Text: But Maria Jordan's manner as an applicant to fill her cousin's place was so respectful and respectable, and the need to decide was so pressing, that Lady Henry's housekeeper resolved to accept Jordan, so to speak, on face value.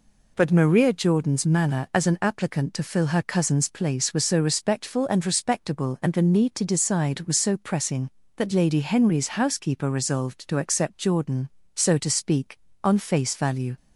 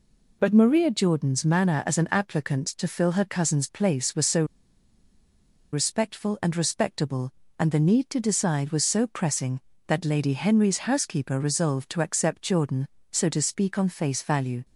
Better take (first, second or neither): first